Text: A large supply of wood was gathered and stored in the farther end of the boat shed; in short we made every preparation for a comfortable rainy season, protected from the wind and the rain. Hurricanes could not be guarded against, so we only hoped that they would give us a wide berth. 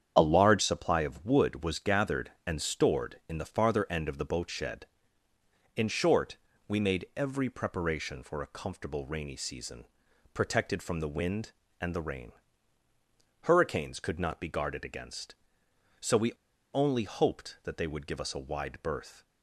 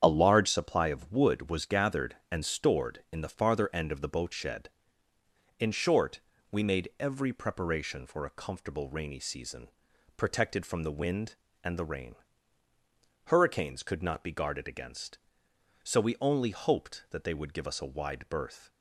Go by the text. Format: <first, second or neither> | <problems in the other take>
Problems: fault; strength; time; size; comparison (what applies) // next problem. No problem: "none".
second | starts louder than the rest; strong; until 1.1 s; 7.5 dB; strong in the second // pauses between "short" and "we"; slight; at 6.3 s; 0.30 s long; slight in the second // pauses between "we" and "only"; at 16.3 s; 0.39 s long